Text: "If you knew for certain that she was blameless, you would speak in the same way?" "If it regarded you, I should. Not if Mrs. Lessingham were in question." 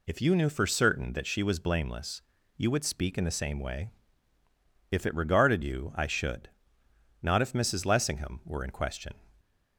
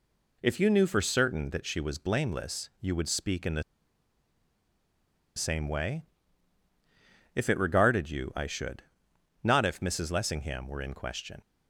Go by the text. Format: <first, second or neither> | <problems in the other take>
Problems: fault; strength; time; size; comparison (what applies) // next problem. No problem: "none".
first | pauses between "the" and "same"; strong; at 3.6 s; 1.7 s long